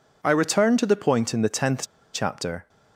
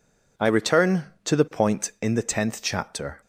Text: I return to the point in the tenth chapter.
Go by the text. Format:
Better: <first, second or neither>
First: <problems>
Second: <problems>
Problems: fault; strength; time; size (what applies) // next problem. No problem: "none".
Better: second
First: pauses between "tenth" and "chapter"; slight; at 1.8 s; 0.30 s long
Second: none